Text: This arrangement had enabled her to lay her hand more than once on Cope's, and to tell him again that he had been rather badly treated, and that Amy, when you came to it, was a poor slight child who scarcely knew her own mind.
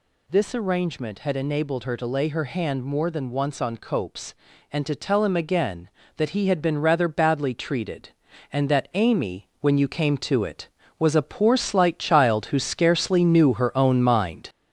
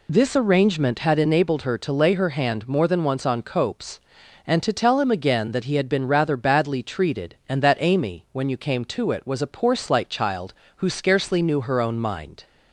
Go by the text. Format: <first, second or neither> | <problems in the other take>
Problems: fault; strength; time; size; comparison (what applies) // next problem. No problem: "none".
second | gets louder; noticeable; throughout; 5 dB